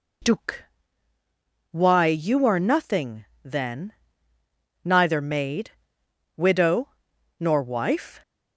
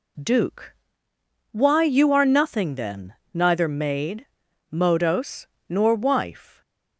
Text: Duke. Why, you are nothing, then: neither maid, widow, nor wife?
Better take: first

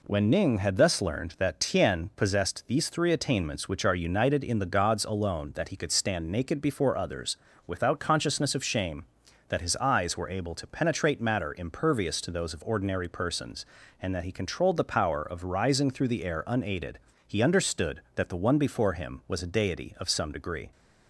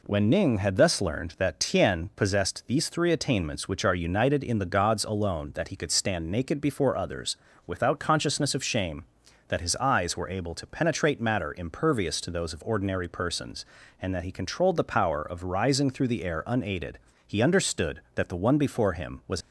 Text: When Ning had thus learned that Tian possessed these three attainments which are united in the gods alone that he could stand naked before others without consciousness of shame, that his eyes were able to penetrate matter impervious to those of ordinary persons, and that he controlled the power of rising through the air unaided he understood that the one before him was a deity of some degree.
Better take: first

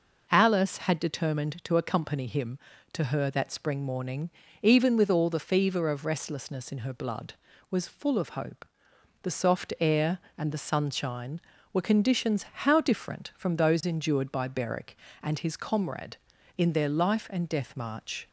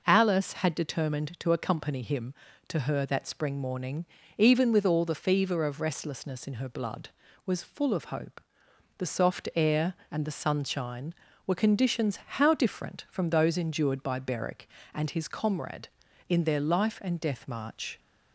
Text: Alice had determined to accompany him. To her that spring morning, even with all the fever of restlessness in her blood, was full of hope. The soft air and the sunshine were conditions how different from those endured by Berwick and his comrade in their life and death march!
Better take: neither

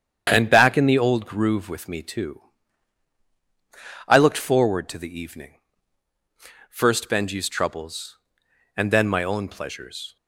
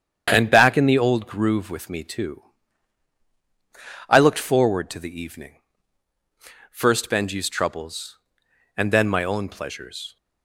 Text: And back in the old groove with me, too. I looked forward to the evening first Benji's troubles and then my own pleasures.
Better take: neither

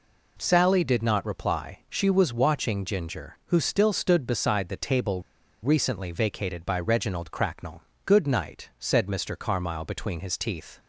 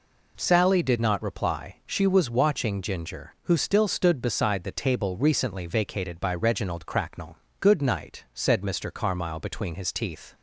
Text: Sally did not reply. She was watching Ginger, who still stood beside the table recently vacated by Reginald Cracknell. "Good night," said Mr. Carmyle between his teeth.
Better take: second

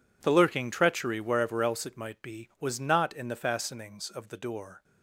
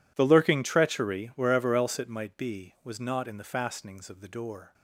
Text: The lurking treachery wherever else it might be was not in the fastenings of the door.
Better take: neither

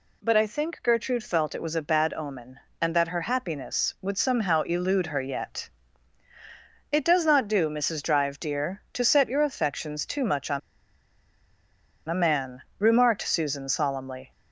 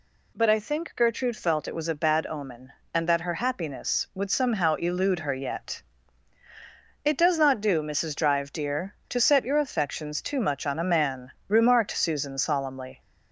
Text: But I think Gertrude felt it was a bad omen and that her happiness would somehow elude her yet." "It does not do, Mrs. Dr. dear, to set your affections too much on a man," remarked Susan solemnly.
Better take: second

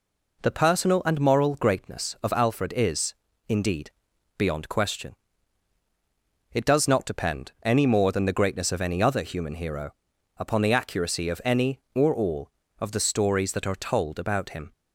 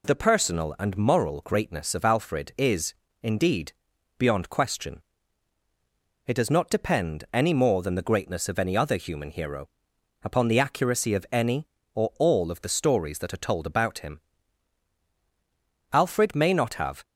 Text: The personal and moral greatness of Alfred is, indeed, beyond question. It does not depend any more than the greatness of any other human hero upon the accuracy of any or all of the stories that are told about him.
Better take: first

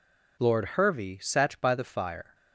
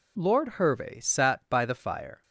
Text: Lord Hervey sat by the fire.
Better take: neither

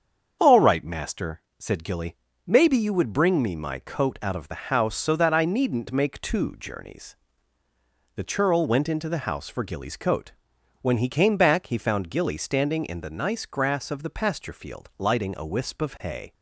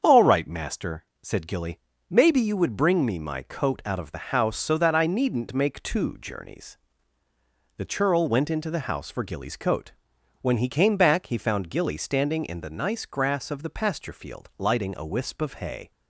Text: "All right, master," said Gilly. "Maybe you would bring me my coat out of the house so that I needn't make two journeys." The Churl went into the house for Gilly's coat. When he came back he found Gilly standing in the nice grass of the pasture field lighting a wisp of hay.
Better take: neither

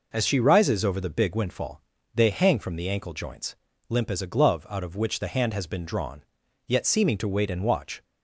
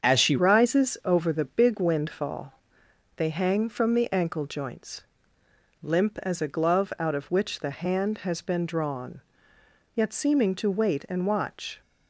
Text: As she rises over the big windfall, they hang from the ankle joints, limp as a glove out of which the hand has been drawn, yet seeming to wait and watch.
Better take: first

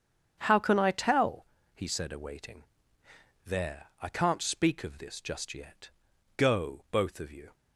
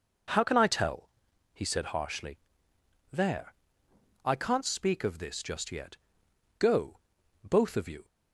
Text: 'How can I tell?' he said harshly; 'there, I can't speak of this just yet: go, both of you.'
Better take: second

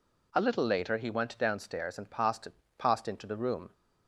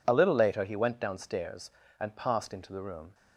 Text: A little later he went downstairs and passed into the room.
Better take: second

